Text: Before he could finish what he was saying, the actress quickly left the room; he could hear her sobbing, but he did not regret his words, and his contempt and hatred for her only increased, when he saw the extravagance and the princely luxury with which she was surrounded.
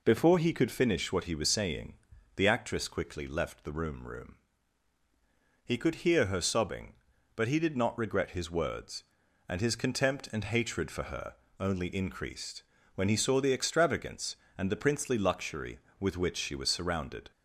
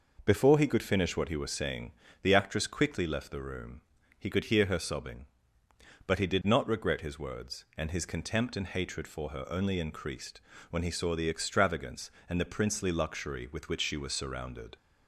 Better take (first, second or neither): second